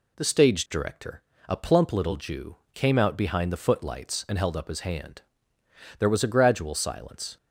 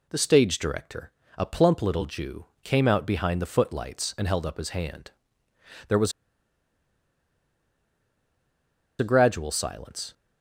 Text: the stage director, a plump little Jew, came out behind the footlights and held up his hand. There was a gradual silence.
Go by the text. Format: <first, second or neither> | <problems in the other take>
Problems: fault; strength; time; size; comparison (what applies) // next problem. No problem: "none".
first | pauses between "was" and "a"; strong; at 6.1 s; 2.8 s long